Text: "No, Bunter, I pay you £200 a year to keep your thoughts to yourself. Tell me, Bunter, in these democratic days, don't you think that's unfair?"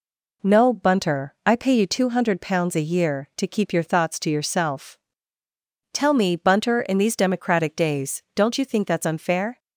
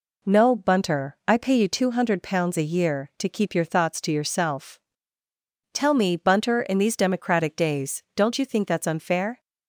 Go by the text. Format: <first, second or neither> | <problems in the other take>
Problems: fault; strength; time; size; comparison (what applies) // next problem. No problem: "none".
neither | none